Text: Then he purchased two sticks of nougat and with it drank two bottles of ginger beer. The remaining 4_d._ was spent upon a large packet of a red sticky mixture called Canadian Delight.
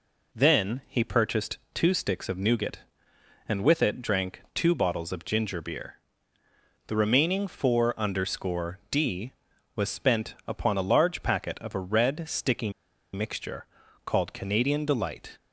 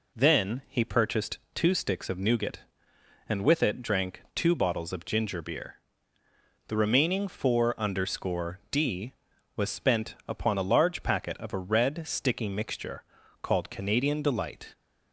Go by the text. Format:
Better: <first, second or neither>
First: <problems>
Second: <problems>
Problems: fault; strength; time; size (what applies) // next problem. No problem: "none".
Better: second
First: pauses between "purchased" and "two"; slight; at 1.5 s; 0.16 s long // pauses between "sticky" and "mixture"; at 12.6 s; 0.43 s long // pauses between "mixture" and "called"; at 13.6 s; 0.40 s long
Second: pauses between "purchased" and "two"; slight; at 1.3 s; 0.16 s long // pauses between "mixture" and "called"; at 13.0 s; 0.39 s long